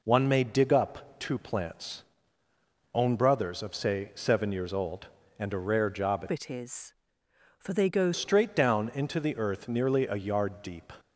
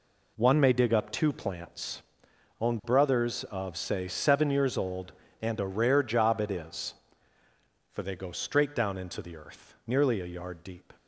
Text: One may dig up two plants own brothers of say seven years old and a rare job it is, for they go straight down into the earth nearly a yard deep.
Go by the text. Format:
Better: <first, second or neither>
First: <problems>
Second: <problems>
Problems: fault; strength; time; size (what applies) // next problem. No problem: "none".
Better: second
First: pauses between "plants" and "own"; noticeable; at 2.0 s; 0.92 s long // changes voice from "it" to "go"; from 6.2 to 8.1 s; 1.9 s long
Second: pauses between "plants" and "own"; noticeable; at 2.0 s; 0.60 s long